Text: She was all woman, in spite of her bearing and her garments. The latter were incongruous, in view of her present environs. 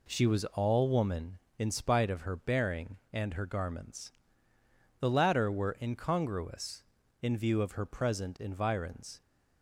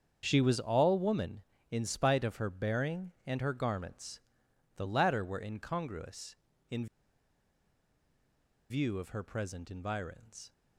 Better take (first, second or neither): first